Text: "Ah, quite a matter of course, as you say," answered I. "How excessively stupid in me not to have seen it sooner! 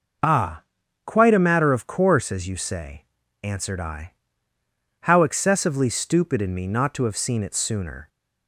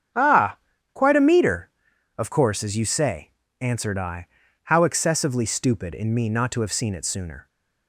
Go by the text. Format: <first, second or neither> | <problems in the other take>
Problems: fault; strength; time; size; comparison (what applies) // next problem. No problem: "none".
first | starts louder than the rest; strong; until 1.5 s; 8 dB // says "meter" for "matter"; at 1.2 s